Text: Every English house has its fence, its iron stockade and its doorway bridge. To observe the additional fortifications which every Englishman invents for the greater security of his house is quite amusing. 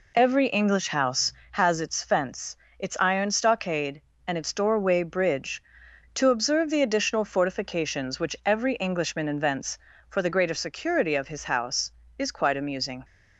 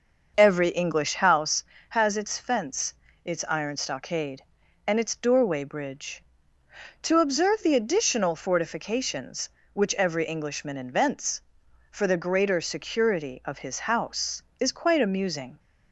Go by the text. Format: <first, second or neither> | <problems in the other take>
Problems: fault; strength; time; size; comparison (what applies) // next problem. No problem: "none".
first | starts louder than the rest; until 1.5 s; 6 dB